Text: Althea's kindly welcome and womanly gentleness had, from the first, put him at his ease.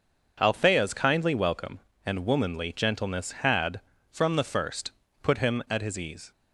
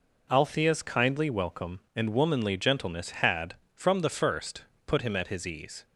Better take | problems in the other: neither | none

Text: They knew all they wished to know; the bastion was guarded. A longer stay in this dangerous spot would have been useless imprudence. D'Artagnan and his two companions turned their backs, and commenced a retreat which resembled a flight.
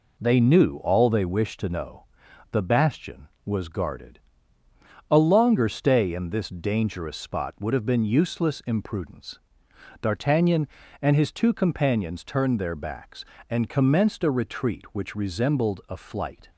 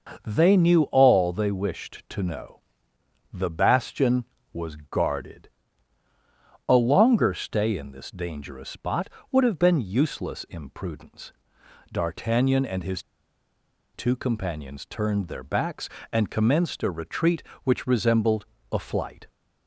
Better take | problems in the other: first | starts louder than the rest; noticeable; until 1.2 s; 6 dB // pauses between "his" and "two"; noticeable; at 13.0 s; 0.92 s long // pauses between "resembled" and "a"; slight; at 18.4 s; 0.28 s long

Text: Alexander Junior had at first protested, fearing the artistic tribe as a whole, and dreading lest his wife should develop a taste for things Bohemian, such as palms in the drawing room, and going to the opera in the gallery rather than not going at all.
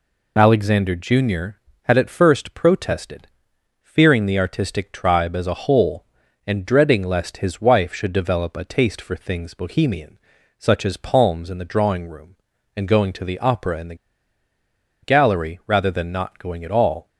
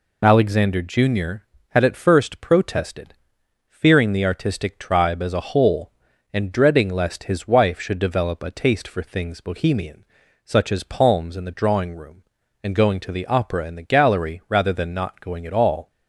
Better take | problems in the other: second | pauses between "the" and "gallery"; at 13.9 s; 1.0 s long

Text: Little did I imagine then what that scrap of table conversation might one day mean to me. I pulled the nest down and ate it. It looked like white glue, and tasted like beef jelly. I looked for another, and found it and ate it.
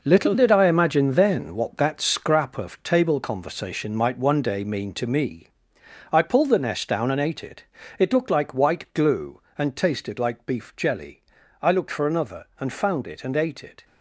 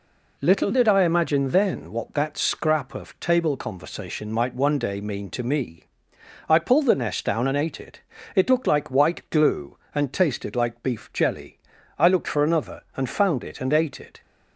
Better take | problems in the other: second | gets quieter; strong; throughout; 9.5 dB

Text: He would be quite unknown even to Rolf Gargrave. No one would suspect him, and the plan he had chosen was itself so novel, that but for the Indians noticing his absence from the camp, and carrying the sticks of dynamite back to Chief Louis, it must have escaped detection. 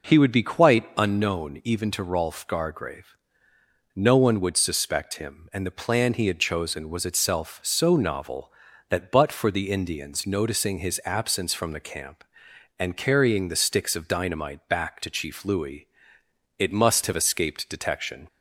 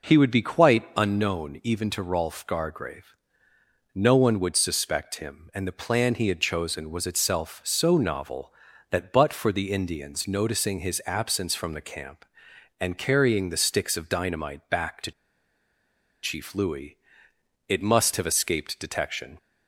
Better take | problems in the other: first | pauses between "to" and "Chief"; at 15.1 s; 1.1 s long

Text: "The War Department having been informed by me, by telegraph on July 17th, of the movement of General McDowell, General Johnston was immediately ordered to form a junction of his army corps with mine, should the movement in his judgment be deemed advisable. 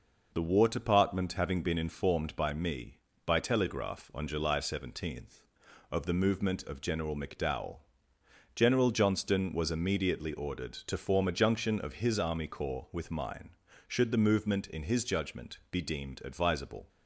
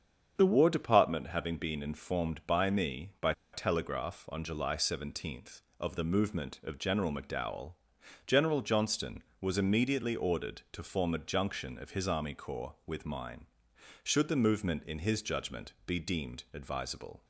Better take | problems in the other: first | starts louder than the rest; strong; until 1.3 s; 7.5 dB // pauses between "by" and "telegraph"; slight; at 3.3 s; 0.21 s long

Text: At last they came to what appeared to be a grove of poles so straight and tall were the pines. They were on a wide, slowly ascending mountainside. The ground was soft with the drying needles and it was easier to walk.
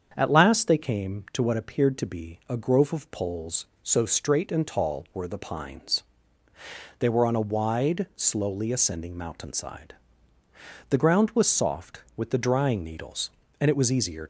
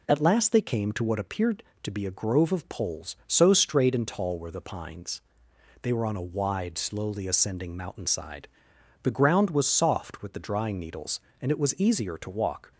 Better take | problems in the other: second | starts louder than the rest; strong; until 1.1 s; 7.5 dB // stops before "to walk"; at 14.2 s

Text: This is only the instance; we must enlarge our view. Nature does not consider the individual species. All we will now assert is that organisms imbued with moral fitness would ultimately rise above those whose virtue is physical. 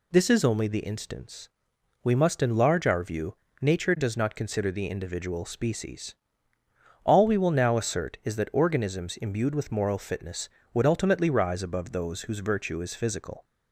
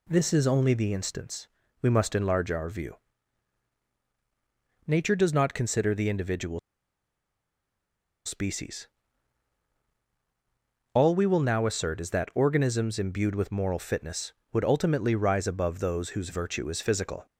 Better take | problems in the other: first | pauses between "individual" and "species"; strong; at 6.5 s; 1.6 s long

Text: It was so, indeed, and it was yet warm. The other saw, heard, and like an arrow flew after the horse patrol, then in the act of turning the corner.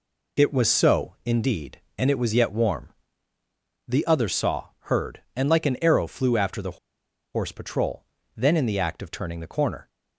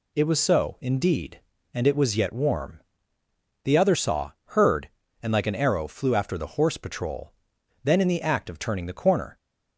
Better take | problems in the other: second | pauses between "the" and "horse"; noticeable; at 6.7 s; 0.56 s long

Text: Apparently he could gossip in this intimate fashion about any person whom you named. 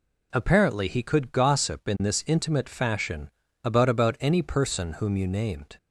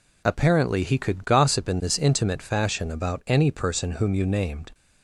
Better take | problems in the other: second | pauses between "fashion" and "about"; slight; at 3.2 s; 0.34 s long // says "about" twice; at 3.8 s

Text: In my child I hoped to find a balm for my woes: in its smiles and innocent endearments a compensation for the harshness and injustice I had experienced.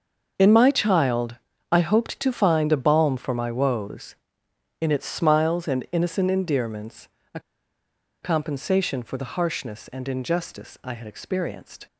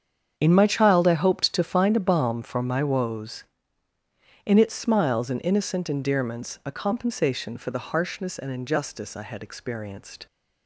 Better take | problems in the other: second | starts louder than the rest; until 1.7 s; 6.5 dB; strong in the second // pauses between "child" and "I"; slight; at 1.3 s; 0.36 s long // pauses between "endearments" and "a"; slight; at 7.0 s; 0.26 s long // pauses between "a" and "compensation"; noticeable; at 7.3 s; 0.82 s long

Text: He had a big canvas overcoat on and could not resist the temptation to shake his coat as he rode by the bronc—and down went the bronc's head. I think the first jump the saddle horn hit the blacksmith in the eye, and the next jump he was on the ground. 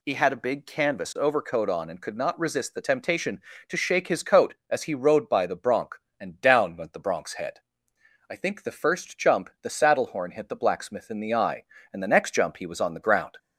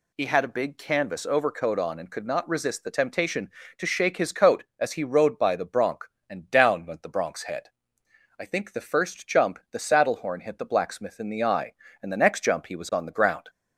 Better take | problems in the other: neither | none

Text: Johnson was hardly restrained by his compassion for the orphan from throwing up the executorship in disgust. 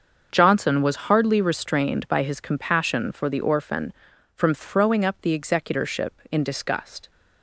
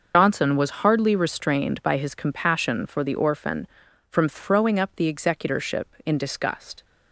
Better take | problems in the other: first | loses the start of "Johnson"; at 0.1 s; 85 ms // starts louder than the rest; until 1.2 s; 6.5 dB; also in the first

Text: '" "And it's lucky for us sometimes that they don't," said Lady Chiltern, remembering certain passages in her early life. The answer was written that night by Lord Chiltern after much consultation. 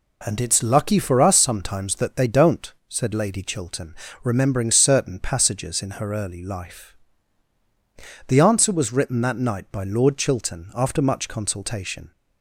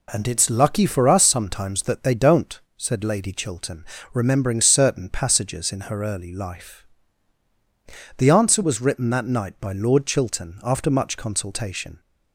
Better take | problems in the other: neither | none

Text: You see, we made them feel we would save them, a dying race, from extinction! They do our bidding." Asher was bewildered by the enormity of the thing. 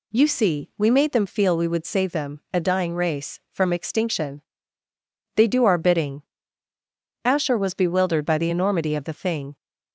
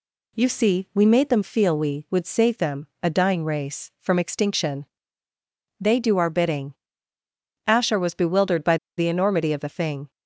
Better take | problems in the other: first | pauses between "by" and "the"; slight; at 8.7 s; 0.20 s long

